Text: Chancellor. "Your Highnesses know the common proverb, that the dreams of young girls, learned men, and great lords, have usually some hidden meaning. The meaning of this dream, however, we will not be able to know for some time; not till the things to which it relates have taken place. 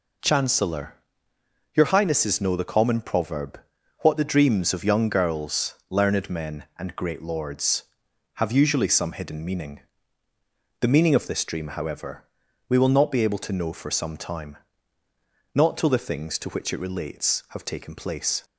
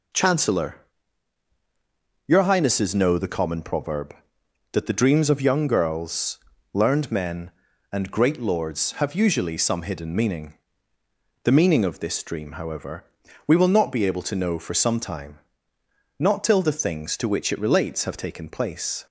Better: second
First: says "what" for "that"; at 4.0 s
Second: none

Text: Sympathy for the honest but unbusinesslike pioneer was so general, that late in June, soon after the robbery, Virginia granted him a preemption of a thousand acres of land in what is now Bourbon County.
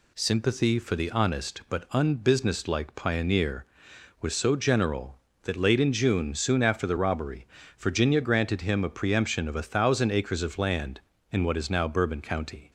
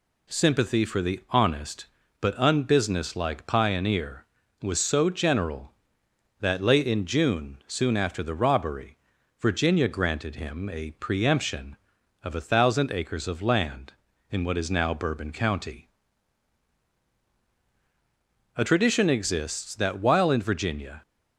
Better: first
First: none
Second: goes on to say "A tradition exists that while in Virginia"; strong; from 18.5 s on; 2.4 s long

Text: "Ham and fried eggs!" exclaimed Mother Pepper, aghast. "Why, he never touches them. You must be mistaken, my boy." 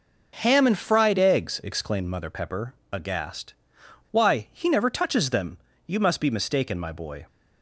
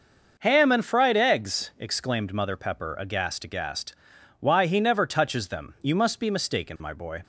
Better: first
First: none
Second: says "aghast" twice; at 3.4 s

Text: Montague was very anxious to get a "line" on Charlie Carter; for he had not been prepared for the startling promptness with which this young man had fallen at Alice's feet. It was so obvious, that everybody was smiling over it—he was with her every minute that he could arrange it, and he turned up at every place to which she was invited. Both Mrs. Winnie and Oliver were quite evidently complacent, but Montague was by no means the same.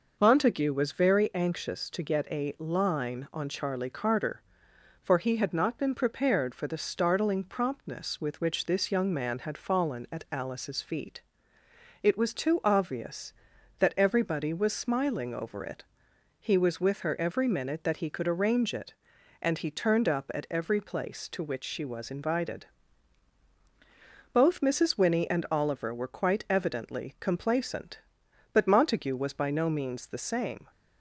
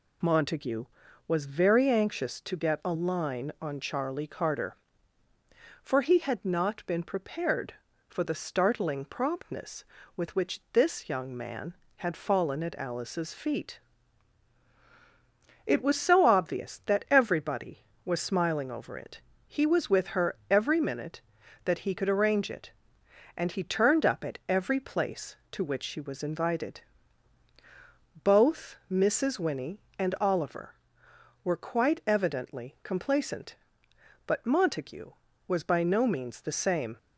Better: second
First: says "too" for "so"; at 12.3 s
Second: none

